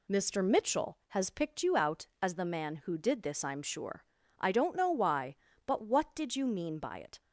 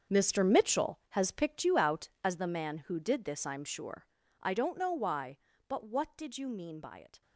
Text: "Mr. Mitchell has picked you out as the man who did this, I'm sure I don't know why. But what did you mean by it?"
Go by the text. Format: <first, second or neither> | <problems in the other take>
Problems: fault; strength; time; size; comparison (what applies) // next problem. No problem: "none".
first | gets quieter; strong; throughout; 13.5 dB // pauses between "sure" and "I"; slight; at 4.0 s; 0.36 s long; slight in the first